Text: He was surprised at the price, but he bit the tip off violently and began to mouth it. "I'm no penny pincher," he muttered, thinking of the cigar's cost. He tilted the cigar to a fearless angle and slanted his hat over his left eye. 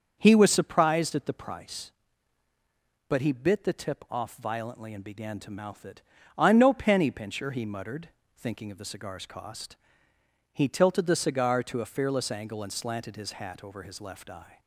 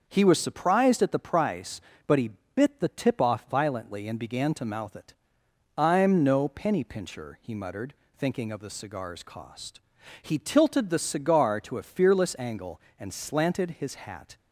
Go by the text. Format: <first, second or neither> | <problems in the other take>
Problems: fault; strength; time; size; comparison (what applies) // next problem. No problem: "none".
first | starts louder than the rest; until 1.0 s; 6.5 dB; also in the first // pauses between "he" and "bit"; slight; at 2.3 s; 0.24 s long // stops before "over his left eye"; at 14.3 s